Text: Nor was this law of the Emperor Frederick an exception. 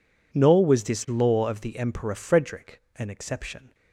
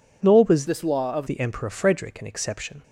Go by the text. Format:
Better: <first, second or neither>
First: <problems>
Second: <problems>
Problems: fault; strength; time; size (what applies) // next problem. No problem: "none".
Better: first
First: none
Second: changes voice from "this" to "of"; from 0.6 to 1.2 s; 0.6 s long